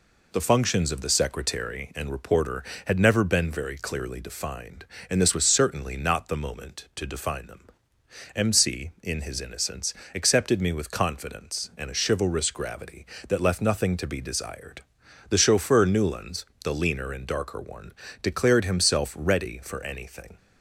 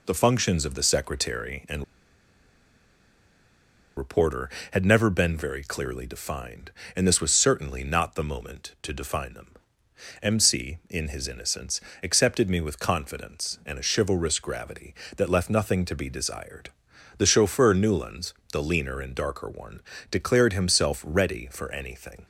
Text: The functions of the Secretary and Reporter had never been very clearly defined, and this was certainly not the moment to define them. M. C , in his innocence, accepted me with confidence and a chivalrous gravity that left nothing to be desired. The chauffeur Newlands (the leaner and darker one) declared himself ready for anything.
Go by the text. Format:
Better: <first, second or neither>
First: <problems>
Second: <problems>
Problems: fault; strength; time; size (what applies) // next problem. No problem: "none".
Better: first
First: none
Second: pauses between "and" and "Reporter"; strong; at 1.8 s; 2.1 s long